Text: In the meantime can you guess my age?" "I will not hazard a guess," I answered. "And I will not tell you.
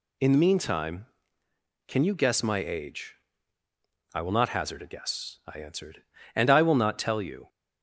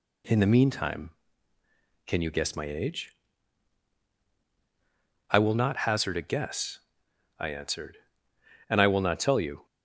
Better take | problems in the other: neither | none

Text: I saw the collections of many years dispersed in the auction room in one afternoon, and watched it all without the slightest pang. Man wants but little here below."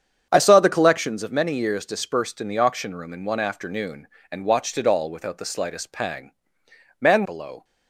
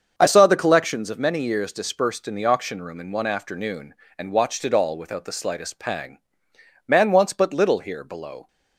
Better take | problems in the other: second | starts louder than the rest; strong; until 1.3 s; 8 dB; also in the second // skips "wants but little here"; at 7.2 s

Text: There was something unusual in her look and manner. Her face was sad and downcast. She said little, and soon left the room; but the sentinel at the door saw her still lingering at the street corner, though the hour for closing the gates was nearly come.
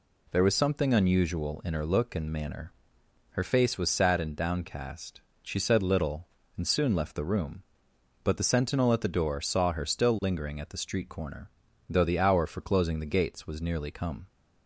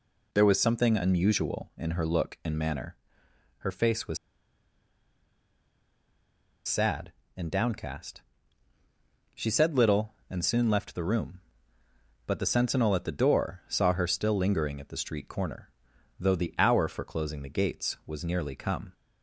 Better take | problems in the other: first | pauses between "was" and "sad"; strong; at 4.1 s; 2.4 s long

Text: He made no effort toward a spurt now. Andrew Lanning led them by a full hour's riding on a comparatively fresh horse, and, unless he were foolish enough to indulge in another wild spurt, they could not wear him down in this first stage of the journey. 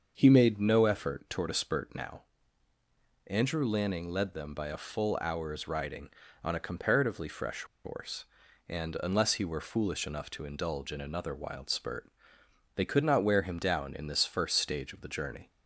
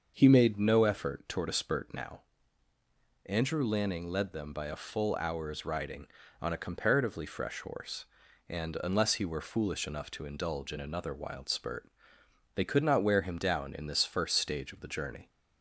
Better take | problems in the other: second | starts louder than the rest; until 1.1 s; 6.5 dB; also in the second // pauses between "fresh" and "horse"; slight; at 7.6 s; 0.20 s long

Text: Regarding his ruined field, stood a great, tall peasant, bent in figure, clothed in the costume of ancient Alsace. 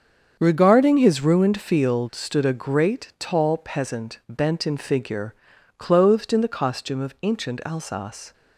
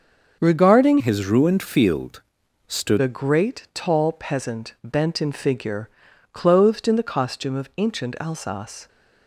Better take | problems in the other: first | starts louder than the rest; until 1.4 s; 6.5 dB; strong in the first // changes voice from "his" to "stood"; from 1.0 to 3.0 s; 2.0 s long

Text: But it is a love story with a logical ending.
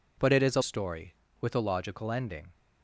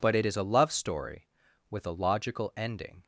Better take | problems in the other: second | skips "love"; at 0.6 s

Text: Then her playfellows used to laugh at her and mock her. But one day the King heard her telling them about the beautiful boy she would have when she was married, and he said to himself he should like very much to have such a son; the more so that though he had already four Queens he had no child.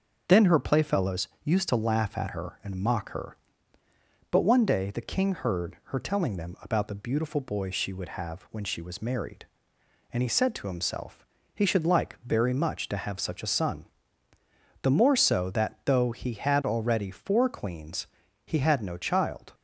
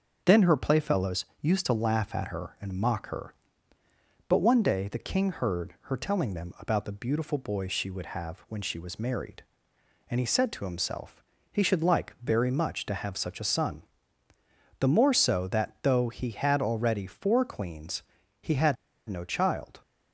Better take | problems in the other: first | starts louder than the rest; until 1.2 s; 6.5 dB; also in the first // pauses between "himself" and "he"; slight; at 11.2 s; 0.30 s long; slight in the first // pauses between "Queens" and "he"; at 18.0 s; 0.38 s long; also in the first // pauses between "had" and "no"; slight; at 18.7 s; 0.33 s long

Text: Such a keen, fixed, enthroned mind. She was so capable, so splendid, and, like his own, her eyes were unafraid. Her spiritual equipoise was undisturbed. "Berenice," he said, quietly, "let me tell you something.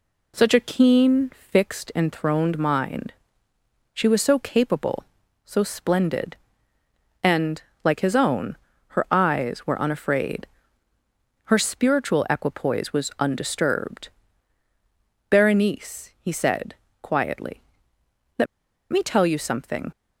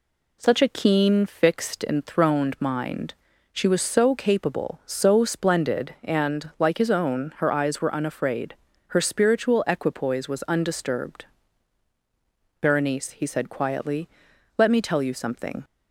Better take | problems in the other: second | pauses between "let" and "me"; noticeable; at 18.4 s; 0.46 s long

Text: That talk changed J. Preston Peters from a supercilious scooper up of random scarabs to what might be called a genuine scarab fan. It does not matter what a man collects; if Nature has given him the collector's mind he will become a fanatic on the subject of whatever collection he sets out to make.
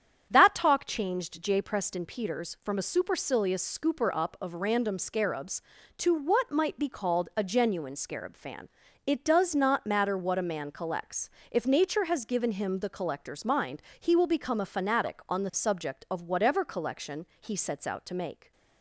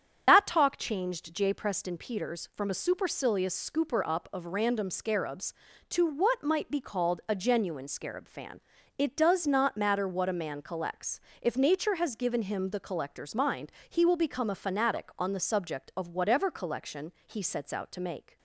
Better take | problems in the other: first | loses the start of "That"; at 0.2 s; 55 ms // starts louder than the rest; strong; until 1.2 s; 8 dB; strong in the first // pauses between "mind" and "he"; slight; at 13.7 s; 0.18 s long; slight in the first

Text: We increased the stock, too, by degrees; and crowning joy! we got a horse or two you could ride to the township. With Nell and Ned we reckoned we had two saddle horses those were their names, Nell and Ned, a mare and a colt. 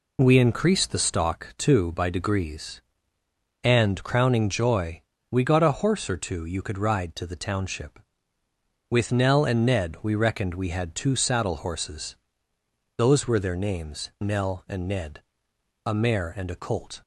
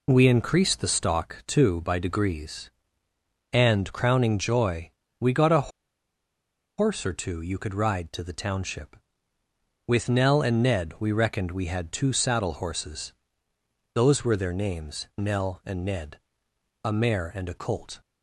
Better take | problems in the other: first | pauses between "a" and "horse"; at 5.6 s; 1.0 s long // pauses between "horses" and "those"; noticeable; at 13.1 s; 0.80 s long; noticeable in the first

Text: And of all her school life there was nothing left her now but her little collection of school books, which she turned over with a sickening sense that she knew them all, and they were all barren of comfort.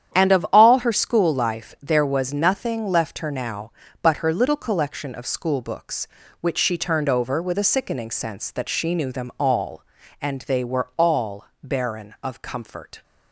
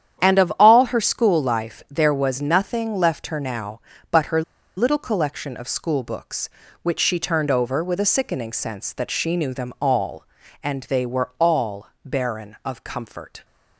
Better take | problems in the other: first | starts louder than the rest; strong; until 1.2 s; 9.5 dB; strong in the first // pauses between "her" and "little"; slight; at 4.4 s; 0.35 s long // pauses between "all" and "barren"; slight; at 11.8 s; 0.18 s long; slight in the first

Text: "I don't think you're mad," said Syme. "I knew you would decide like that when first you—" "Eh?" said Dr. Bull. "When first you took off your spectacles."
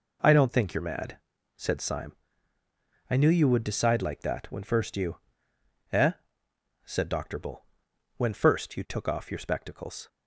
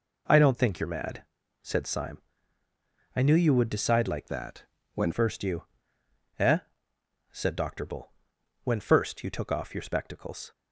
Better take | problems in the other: first | changes voice from "that" to "when"; from 4.2 to 5.1 s; 0.9 s long // pauses between "that" and "when"; slight; at 4.6 s; 0.32 s long

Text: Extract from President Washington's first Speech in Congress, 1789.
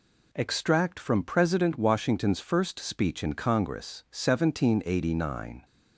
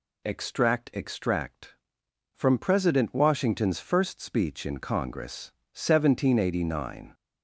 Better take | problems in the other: first | says "Extract" twice; at 0.9 s

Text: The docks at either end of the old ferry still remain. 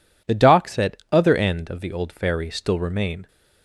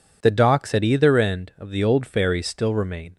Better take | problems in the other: second | says "other" for "either"; at 1.1 s

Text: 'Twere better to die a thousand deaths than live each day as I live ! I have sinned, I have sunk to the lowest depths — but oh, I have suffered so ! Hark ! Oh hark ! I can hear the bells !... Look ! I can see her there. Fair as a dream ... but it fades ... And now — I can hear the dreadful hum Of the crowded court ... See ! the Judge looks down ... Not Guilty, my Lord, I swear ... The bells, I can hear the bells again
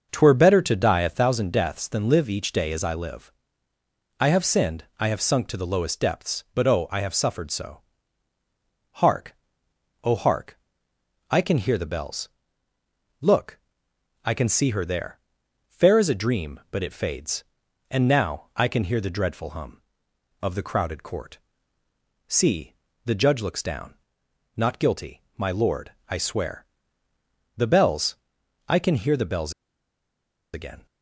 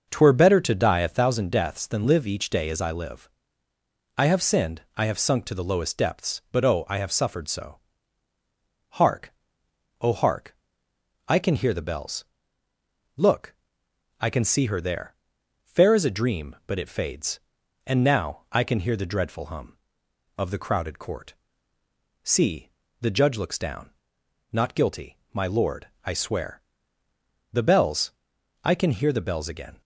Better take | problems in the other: second | starts louder than the rest; noticeable; until 1.1 s; 6 dB; noticeable in the second // pauses between "bells" and "again"; at 29.5 s; 1.0 s long

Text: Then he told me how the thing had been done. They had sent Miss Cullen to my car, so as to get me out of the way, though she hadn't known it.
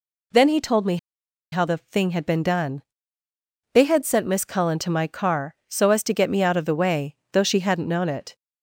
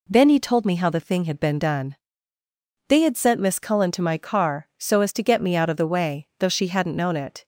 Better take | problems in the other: second | pauses between "me" and "how"; noticeable; at 0.9 s; 0.55 s long

